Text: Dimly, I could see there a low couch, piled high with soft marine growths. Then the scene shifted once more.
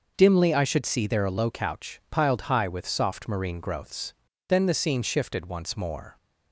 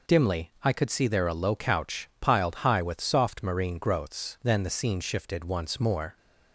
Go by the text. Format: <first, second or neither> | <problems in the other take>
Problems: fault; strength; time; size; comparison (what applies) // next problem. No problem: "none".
second | starts louder than the rest; noticeable; until 1.1 s; 6 dB // says "should" for "could"; at 0.6 s